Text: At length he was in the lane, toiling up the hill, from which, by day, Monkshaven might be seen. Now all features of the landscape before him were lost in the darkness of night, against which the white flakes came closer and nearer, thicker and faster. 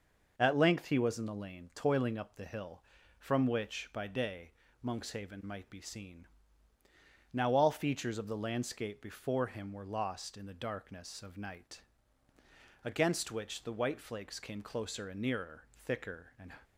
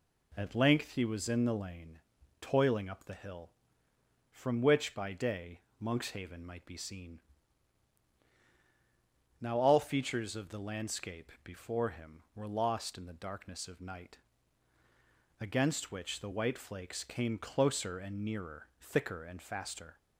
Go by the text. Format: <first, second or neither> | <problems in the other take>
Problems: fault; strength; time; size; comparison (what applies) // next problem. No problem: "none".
second | stops before "faster"; at 16.6 s